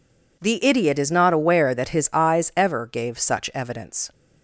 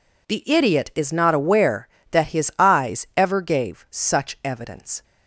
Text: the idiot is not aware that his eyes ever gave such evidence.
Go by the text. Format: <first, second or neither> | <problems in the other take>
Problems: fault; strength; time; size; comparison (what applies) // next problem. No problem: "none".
neither | none